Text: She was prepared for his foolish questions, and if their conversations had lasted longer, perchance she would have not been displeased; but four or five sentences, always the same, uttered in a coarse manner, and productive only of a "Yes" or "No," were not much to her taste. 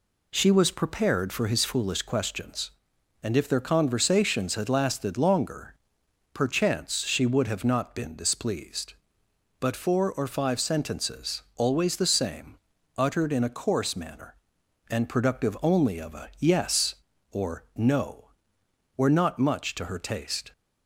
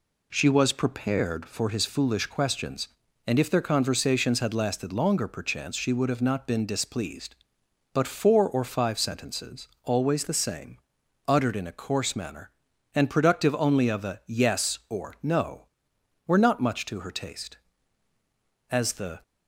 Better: first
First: none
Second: goes on to say "As the"; from 18.7 s on; 0.52 s long

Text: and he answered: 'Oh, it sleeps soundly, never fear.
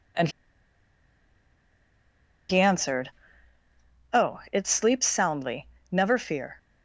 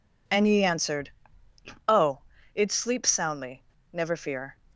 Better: second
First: pauses between "and" and "he"; strong; at 0.2 s; 2.1 s long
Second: none

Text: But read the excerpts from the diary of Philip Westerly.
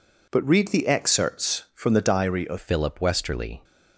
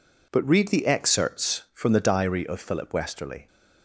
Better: second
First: changes voice at "Philip"; from 2.5 s on; 1.1 s long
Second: none

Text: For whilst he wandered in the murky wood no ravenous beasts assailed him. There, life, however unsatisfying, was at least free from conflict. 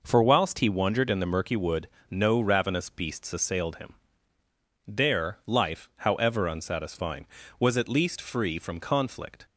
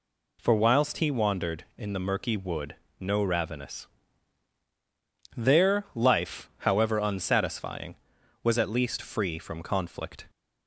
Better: first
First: pauses between "wood" and "no"; slight; at 1.8 s; 0.22 s long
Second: pauses between "wood" and "no"; slight; at 2.7 s; 0.24 s long // skips "beasts assailed him"; at 4.6 s

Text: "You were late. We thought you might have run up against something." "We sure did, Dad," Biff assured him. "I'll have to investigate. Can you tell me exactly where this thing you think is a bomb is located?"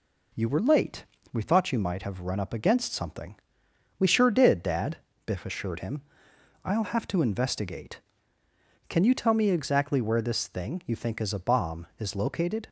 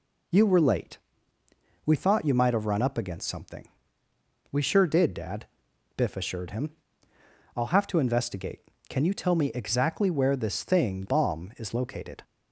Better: first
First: none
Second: skips "you think is a"; at 11.0 s

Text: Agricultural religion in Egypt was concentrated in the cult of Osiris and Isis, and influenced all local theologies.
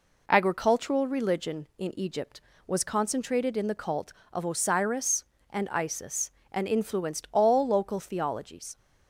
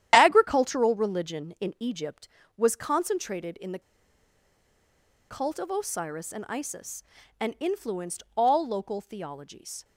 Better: first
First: none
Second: starts louder than the rest; strong; until 1.1 s; 11 dB // pauses between "the" and "cult"; strong; at 3.8 s; 1.4 s long

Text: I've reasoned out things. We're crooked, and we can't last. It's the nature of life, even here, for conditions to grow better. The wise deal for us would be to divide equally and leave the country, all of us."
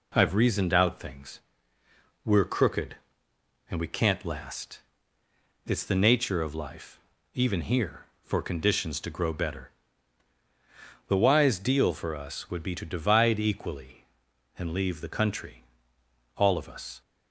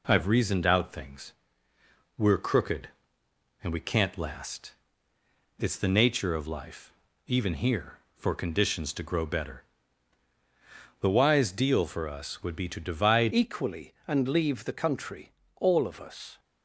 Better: first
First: none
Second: changes voice at "equally"; from 13.3 s on; 3.0 s long

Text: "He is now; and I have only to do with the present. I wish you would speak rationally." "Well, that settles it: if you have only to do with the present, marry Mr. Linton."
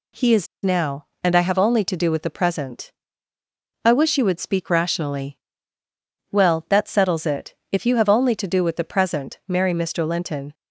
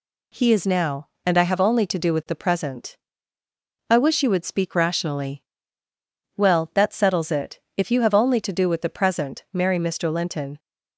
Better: second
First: pauses between "is" and "now"; slight; at 0.4 s; 0.17 s long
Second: none

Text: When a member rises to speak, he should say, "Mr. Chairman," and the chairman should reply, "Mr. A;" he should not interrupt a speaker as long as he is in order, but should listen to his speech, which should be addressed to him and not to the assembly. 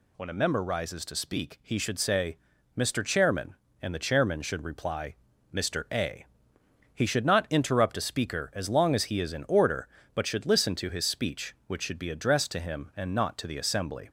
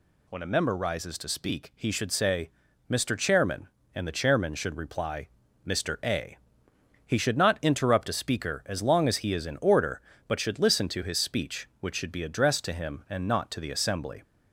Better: neither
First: none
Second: none

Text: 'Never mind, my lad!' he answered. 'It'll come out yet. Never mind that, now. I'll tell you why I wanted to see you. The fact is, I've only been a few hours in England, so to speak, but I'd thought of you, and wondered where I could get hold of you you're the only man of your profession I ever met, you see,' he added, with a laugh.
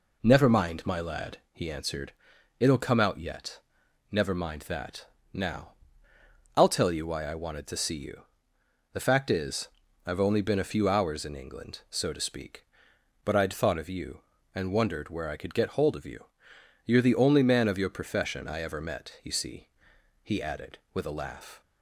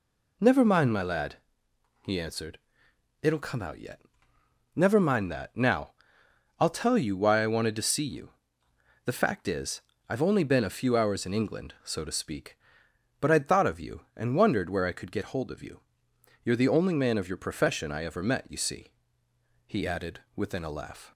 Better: first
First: pauses between "you" and "you're"; noticeable; at 16.2 s; 0.60 s long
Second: pauses between "you" and "you're"; noticeable; at 15.7 s; 0.64 s long // says "within" for "with"; at 20.3 s

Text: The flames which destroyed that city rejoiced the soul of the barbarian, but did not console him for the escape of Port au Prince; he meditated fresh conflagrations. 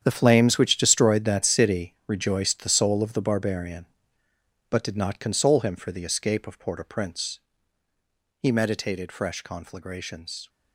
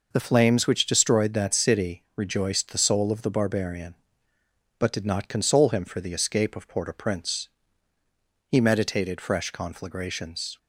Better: second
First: gets quieter; strong; throughout; 13.5 dB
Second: none

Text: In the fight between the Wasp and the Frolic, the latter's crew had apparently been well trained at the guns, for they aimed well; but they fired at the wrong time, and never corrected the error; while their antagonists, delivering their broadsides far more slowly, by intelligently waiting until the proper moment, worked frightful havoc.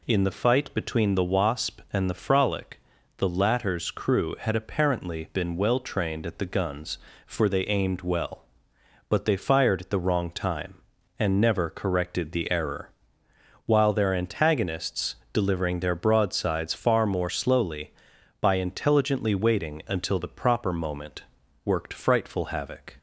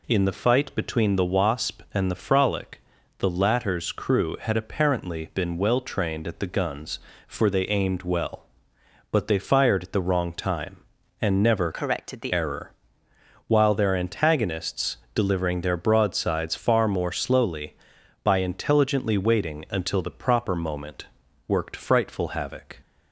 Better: first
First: none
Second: changes voice from "corrected" to "the"; from 11.7 to 12.3 s; 0.6 s long

